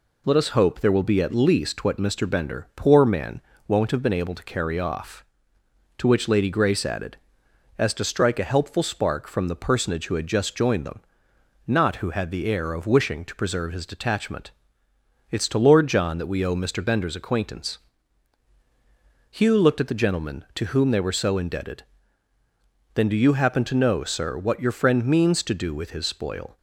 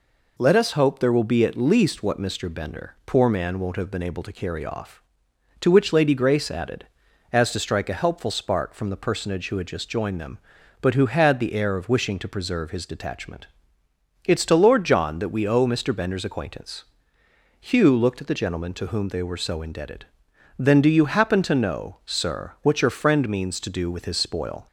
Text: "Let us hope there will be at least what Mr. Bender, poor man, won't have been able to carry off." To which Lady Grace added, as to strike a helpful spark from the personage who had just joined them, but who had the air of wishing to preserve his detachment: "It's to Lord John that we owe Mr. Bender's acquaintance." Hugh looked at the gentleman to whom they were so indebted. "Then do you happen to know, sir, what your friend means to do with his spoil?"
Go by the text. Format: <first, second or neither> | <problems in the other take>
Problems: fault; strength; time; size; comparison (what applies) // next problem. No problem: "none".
second | says "not" for "but"; at 11.6 s